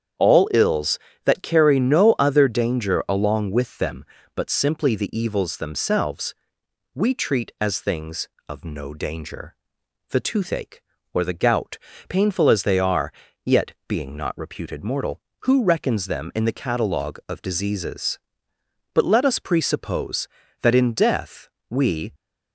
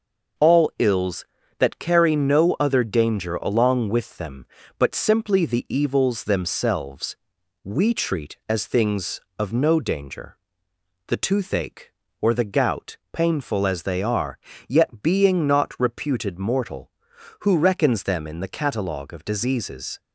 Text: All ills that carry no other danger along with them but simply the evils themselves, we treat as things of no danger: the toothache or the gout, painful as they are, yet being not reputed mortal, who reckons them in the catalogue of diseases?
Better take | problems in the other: second | starts louder than the rest; strong; until 1.5 s; 8 dB // goes on to say "But let us presuppose that in death we"; strong; from 18.9 s on; 3.2 s long

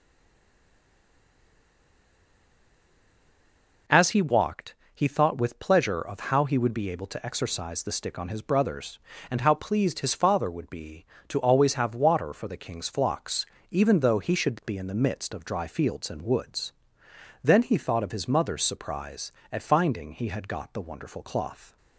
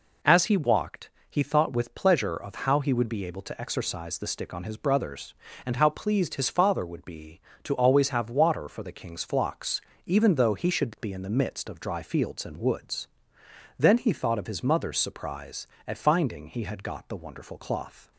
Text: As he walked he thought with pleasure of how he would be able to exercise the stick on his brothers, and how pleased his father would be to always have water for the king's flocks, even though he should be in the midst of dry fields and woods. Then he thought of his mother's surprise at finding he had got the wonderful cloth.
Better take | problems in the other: second | stays silent before the first word; strong; until 3.8 s; 3.8 s long // pauses between "walked" and "he"; slight; at 4.7 s; 0.18 s long; slight in the second

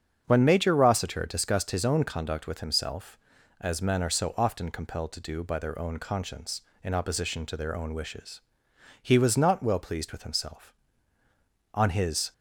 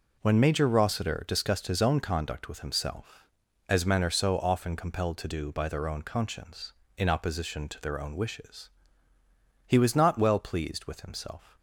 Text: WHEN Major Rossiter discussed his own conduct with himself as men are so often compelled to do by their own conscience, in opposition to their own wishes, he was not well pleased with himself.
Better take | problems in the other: second | starts louder than the rest; strong; until 1.2 s; 7.5 dB // goes on to say "On his"; from 11.7 s on; 0.60 s long

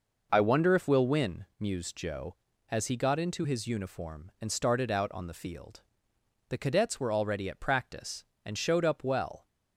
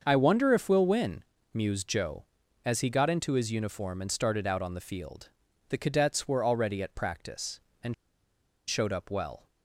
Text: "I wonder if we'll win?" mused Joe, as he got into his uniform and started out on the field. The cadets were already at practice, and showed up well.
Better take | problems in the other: first | starts louder than the rest; until 1.0 s; 6.5 dB // pauses between "and" and "showed"; noticeable; at 7.9 s; 0.74 s long

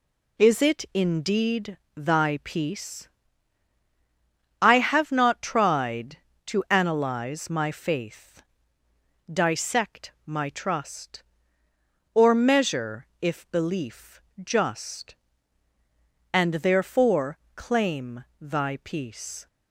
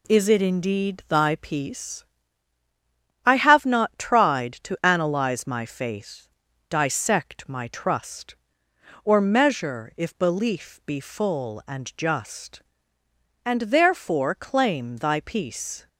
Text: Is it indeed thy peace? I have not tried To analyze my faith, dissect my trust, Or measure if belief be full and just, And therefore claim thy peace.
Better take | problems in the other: second | pauses between "indeed" and "thy"; slight; at 1.7 s; 0.18 s long // skips "be full and"; at 14.3 s // pauses between "therefore" and "claim"; slight; at 17.3 s; 0.18 s long // pauses between "claim" and "thy"; slight; at 18.2 s; 0.16 s long

